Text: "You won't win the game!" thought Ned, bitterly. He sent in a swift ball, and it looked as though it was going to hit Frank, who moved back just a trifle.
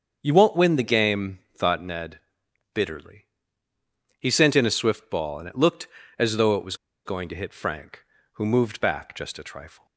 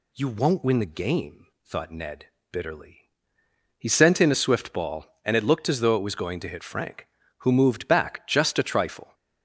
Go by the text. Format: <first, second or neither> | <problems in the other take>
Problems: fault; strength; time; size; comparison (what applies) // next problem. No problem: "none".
second | starts louder than the rest; until 1.2 s; 7 dB // pauses between "was" and "going"; slight; at 6.7 s; 0.27 s long